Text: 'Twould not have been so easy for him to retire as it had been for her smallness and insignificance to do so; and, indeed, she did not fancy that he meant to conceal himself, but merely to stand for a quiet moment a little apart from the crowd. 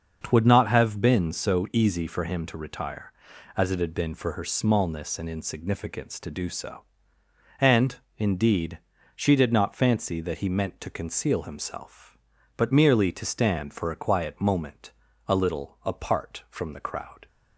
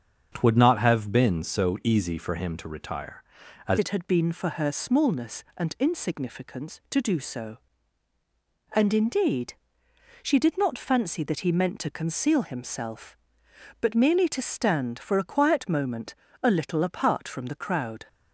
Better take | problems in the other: first | starts louder than the rest; strong; until 1.3 s; 7 dB; also in the first // changes voice at "it"; from 3.7 s on; 14.3 s long // pauses between "moment" and "a"; slight; at 16.1 s; 0.28 s long; slight in the first

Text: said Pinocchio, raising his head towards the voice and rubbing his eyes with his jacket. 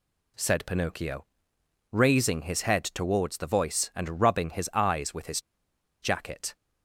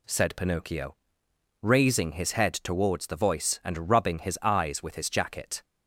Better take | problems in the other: second | pauses between "his" and "jacket"; noticeable; at 5.4 s; 0.61 s long

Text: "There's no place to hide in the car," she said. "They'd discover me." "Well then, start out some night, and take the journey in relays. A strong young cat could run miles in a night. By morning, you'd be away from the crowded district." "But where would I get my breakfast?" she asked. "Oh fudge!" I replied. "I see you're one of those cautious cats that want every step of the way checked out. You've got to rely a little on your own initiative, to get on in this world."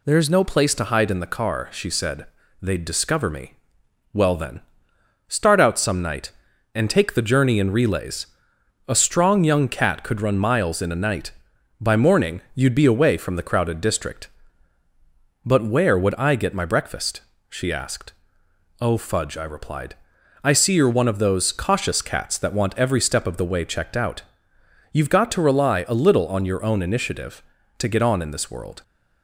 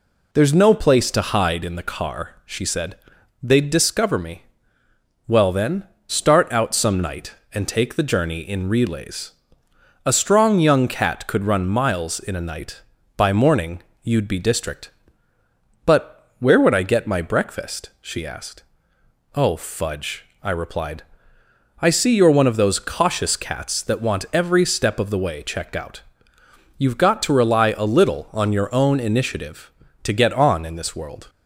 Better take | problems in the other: first | skips "away from the crowded"; at 14.3 s

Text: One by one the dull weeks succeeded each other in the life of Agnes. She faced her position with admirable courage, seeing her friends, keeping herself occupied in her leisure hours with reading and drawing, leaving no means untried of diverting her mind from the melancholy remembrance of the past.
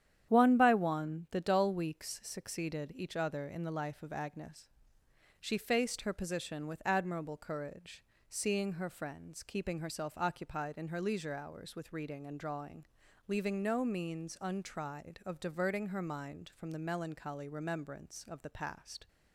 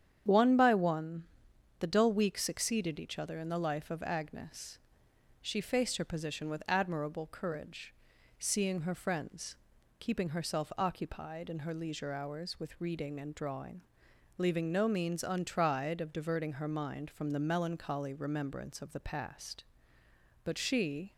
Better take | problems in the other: first | starts louder than the rest; strong; until 1.8 s; 9 dB; strong in the first // pauses between "one" and "the"; noticeable; at 1.2 s; 0.56 s long // goes on to say "But she"; noticeable; from 20.4 s on; 0.70 s long

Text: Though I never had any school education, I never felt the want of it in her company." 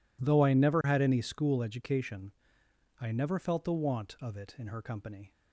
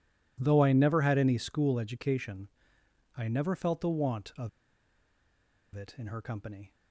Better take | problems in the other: first | pauses between "of" and "it"; strong; at 4.4 s; 1.2 s long

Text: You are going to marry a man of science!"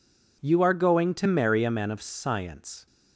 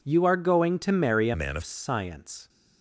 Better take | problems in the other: first | changes voice from "man" to "of"; from 1.3 to 1.6 s; 0.3 s long

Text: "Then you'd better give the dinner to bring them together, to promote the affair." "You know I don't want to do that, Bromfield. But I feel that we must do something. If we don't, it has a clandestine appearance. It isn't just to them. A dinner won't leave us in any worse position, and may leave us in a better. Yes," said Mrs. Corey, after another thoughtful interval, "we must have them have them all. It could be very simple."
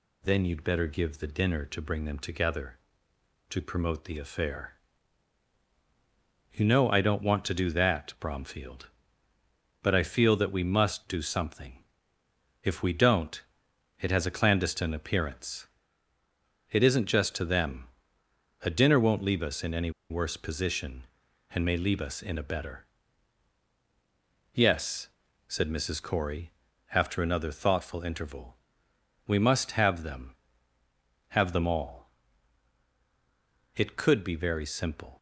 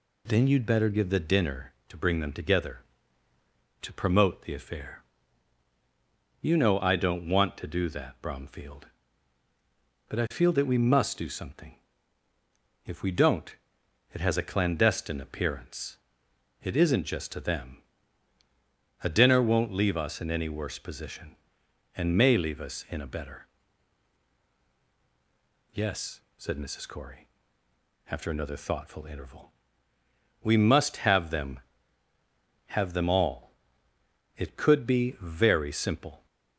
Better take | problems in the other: second | pauses between "any" and "worse"; slight; at 19.8 s; 0.20 s long

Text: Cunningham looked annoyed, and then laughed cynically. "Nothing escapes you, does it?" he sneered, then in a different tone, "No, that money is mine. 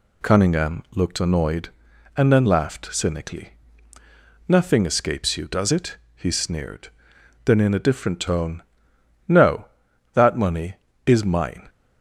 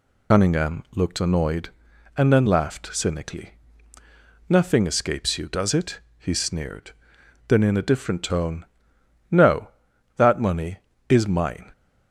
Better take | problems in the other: first | loses the start of "Cunningham"; at 0.3 s; 80 ms

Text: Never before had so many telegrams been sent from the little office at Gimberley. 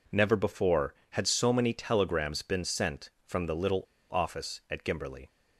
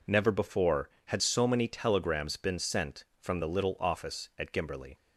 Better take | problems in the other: second | pauses between "little" and "office"; slight; at 3.8 s; 0.30 s long

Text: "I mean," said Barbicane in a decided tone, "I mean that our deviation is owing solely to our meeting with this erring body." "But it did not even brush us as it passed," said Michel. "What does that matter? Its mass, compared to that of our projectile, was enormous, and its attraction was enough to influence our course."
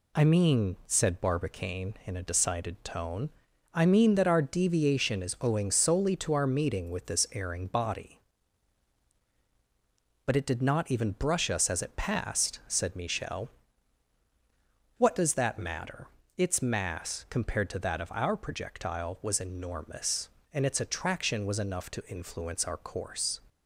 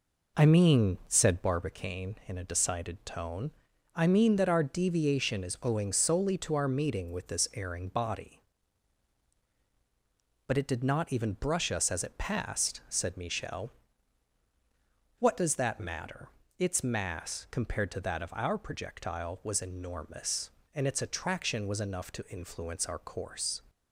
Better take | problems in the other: first | starts louder than the rest; noticeable; until 1.6 s; 4 dB

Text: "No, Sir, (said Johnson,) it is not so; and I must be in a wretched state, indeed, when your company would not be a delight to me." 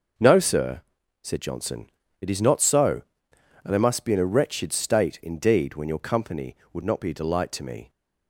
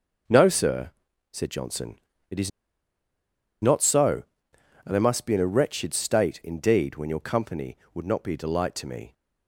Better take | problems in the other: first | pauses between "is" and "not"; at 2.4 s; 1.1 s long

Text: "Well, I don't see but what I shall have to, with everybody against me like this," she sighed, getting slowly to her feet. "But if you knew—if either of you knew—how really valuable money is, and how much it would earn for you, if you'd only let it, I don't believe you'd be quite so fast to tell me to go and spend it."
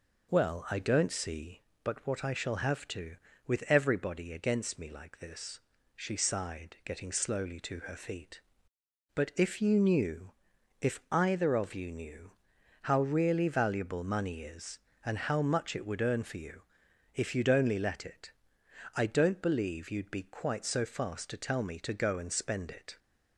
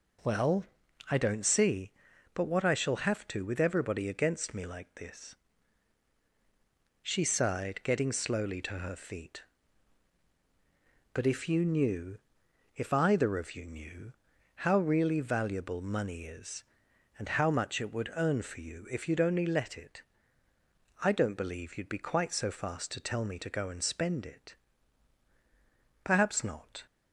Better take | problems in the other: first | goes on to say "Perhaps not"; noticeable; from 26.0 s on; 0.80 s long

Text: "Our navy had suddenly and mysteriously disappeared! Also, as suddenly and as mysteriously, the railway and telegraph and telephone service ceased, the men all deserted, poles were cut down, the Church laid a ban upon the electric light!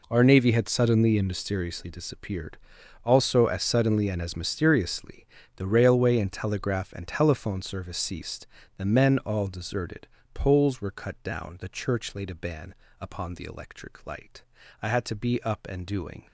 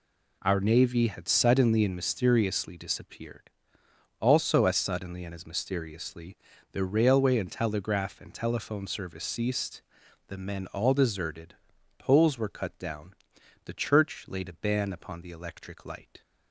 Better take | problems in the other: second | pauses between "ban" and "upon"; slight; at 12.7 s; 0.26 s long // goes on to say "I had to be up and doing"; from 14.8 s on; 1.4 s long

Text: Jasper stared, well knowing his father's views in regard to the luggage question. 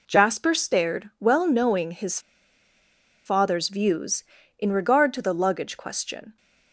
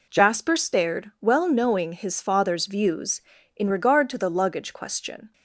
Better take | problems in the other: second | pauses between "his" and "father's"; at 2.1 s; 1.0 s long

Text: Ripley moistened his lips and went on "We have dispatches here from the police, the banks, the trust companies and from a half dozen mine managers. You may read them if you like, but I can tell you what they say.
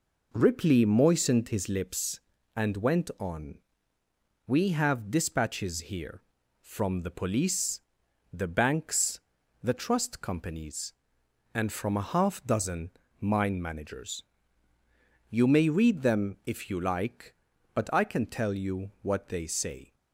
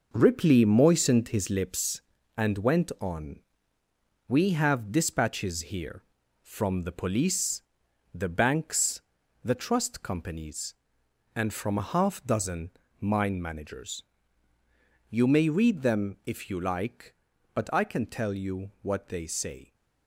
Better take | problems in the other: first | gets quieter; strong; throughout; 7.5 dB // pauses between "on" and "We"; noticeable; at 3.3 s; 0.88 s long; noticeable in the first // pauses between "dozen" and "mine"; slight; at 12.7 s; 0.28 s long; slight in the first

